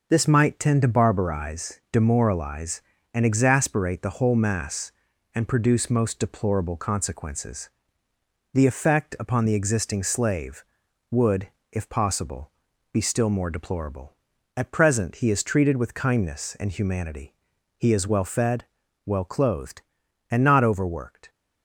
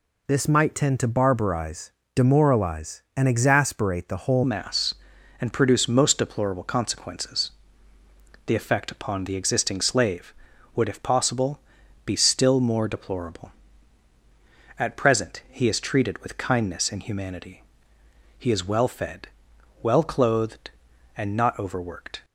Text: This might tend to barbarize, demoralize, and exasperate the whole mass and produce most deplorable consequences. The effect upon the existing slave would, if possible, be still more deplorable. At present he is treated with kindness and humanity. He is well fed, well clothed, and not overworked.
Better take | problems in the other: first | changes voice at "mass"; from 4.4 s on; 17.8 s long

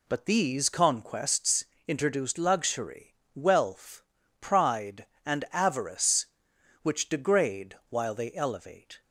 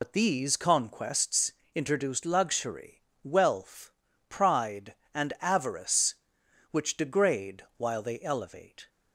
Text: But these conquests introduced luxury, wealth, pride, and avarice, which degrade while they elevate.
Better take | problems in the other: first | loses the start of "But"; at 0.0 s; 60 ms // pauses between "conquests" and "introduced"; slight; at 1.5 s; 0.20 s long; slight in the first

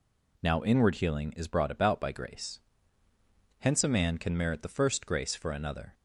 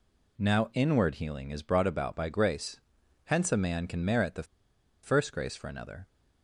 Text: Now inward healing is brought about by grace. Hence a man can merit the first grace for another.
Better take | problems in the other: first | pauses between "the" and "first"; noticeable; at 4.4 s; 0.59 s long

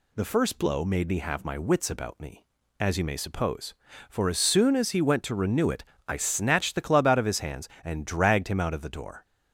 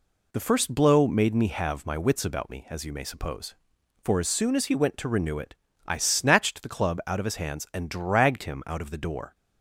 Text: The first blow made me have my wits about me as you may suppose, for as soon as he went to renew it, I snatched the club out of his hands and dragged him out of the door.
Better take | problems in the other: neither | none

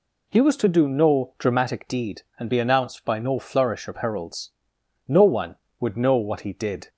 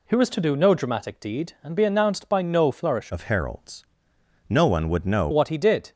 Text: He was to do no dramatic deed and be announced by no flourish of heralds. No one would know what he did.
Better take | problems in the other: first | changes voice from "of" to "know"; from 3.1 to 5.2 s; 2.1 s long

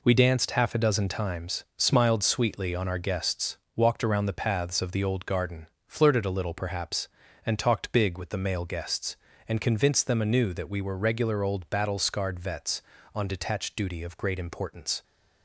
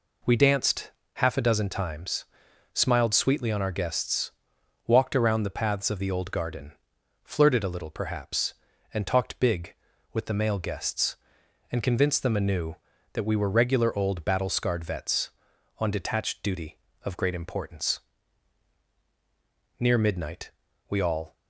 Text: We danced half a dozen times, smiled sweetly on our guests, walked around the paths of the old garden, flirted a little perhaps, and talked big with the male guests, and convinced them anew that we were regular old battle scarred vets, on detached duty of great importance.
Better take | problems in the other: first | pauses between "danced" and "half"; slight; at 0.9 s; 0.22 s long // goes on to say "Near midnight we all"; from 19.8 s on; 1.5 s long

